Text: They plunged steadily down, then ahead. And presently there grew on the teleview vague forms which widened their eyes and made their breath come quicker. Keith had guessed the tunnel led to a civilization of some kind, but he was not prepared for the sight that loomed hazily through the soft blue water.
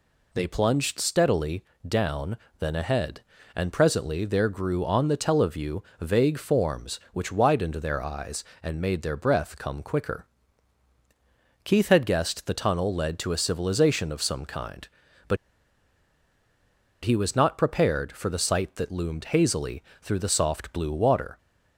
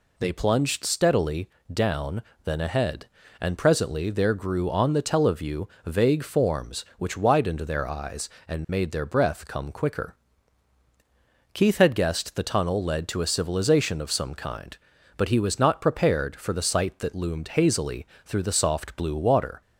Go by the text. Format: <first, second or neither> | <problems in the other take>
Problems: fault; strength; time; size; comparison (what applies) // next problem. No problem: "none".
second | pauses between "steadily" and "down"; slight; at 1.6 s; 0.24 s long; slight in the second // pauses between "teleview" and "vague"; slight; at 5.8 s; 0.18 s long; slight in the second // pauses between "but" and "he"; strong; at 15.3 s; 1.6 s long // pauses between "hazily" and "through"; slight; at 19.8 s; 0.20 s long; slight in the second